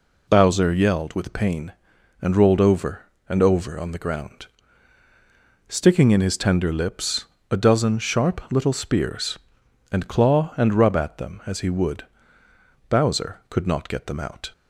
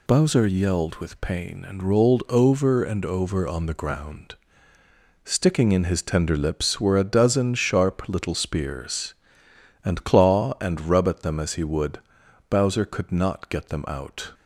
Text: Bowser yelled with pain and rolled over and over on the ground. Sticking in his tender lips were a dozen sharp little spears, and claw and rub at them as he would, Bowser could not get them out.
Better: second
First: skips "were"; at 7.3 s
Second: none

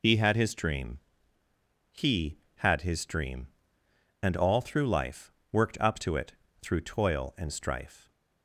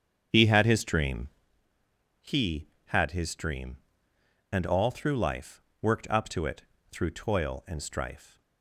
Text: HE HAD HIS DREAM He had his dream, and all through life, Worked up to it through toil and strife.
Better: first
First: pauses between "DREAM" and "He"; noticeable; at 0.9 s; 0.92 s long // pauses between "it" and "through"; slight; at 6.3 s; 0.26 s long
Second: starts louder than the rest; strong; until 1.5 s; 7.5 dB // pauses between "DREAM" and "He"; noticeable; at 1.2 s; 0.92 s long // pauses between "it" and "through"; slight; at 6.6 s; 0.26 s long

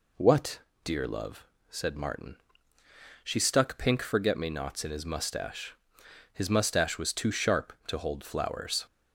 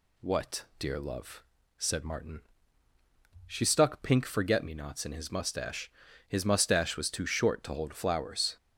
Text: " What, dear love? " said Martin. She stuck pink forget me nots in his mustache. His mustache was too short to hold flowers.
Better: second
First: says "sharp" for "short"; at 7.3 s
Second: none

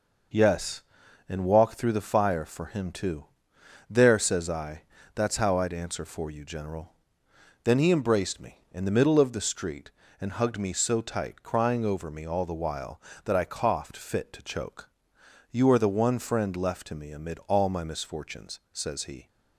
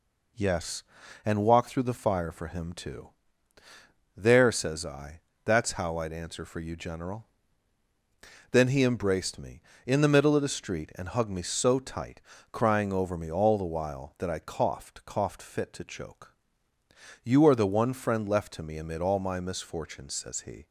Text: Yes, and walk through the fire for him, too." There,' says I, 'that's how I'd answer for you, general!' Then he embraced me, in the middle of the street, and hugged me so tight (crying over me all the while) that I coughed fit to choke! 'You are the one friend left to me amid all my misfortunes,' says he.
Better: first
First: none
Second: says "coughed" twice; at 15.0 s

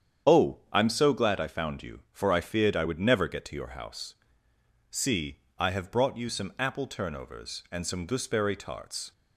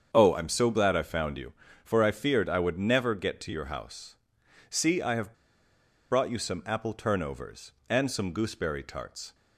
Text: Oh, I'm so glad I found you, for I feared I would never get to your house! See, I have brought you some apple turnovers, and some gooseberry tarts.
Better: first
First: starts louder than the rest; strong; until 1.4 s; 8.5 dB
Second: starts louder than the rest; strong; until 1.1 s; 7 dB // pauses between "have" and "brought"; noticeable; at 5.3 s; 0.77 s long

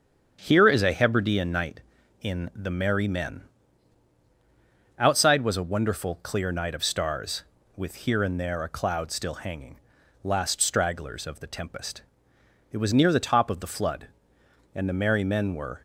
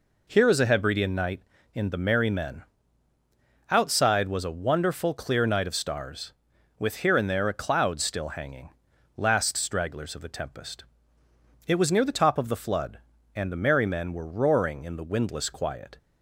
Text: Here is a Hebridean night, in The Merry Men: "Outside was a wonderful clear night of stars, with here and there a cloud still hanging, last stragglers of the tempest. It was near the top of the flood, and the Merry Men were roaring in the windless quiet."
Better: second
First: starts louder than the rest; strong; until 1.4 s; 8 dB // stops before "roaring in the windless quiet"; at 15.7 s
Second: none

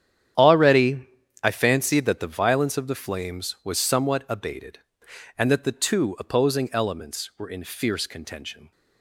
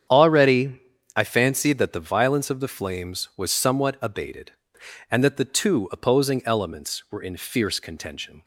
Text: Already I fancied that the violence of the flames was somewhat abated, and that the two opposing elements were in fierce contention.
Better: second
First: gets quieter; strong; throughout; 13.5 dB // starts louder than the rest; strong; until 1.7 s; 9.5 dB // pauses between "Already" and "I"; slight; at 1.0 s; 0.36 s long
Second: starts louder than the rest; strong; until 1.4 s; 8.5 dB // pauses between "Already" and "I"; slight; at 0.7 s; 0.36 s long

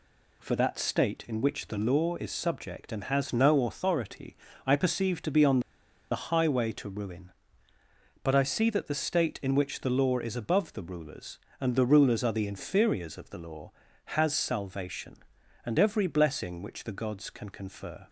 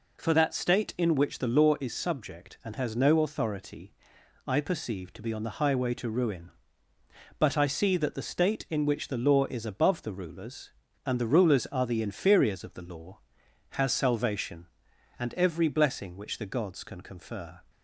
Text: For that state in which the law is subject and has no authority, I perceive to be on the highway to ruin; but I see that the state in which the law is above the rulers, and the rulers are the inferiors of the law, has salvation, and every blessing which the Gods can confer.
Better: second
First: pauses between "on" and "the"; noticeable; at 5.5 s; 0.52 s long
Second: none

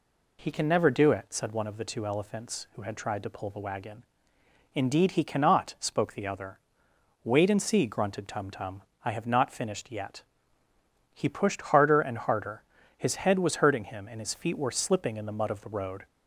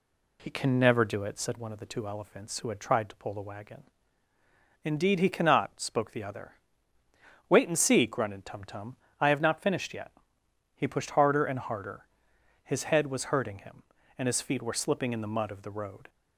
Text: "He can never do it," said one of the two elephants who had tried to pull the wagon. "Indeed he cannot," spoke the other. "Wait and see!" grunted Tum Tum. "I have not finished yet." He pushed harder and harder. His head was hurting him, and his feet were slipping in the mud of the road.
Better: neither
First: none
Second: none

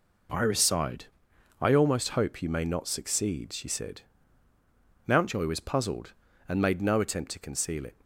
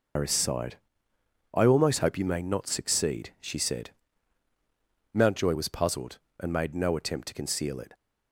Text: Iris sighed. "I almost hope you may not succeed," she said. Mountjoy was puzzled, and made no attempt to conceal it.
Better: first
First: none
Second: loses the start of "Iris"; at 0.1 s; 120 ms

